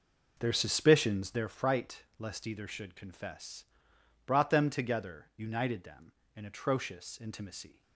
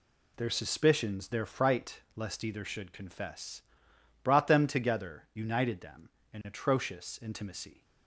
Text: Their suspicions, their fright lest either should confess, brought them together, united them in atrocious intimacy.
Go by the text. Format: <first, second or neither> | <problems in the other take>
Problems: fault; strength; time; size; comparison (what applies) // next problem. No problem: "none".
second | starts louder than the rest; noticeable; until 1.5 s; 5.5 dB // pauses between "fright" and "lest"; slight; at 2.0 s; 0.16 s long; slight in the second